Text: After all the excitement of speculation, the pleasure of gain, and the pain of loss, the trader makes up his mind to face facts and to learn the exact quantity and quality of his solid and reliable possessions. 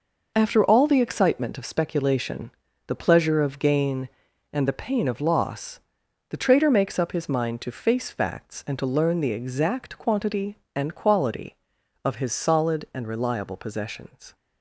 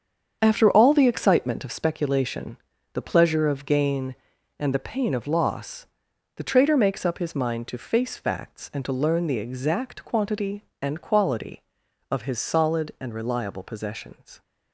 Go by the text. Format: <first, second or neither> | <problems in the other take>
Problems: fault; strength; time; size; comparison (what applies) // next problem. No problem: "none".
first | starts louder than the rest; strong; until 2.0 s; 7.5 dB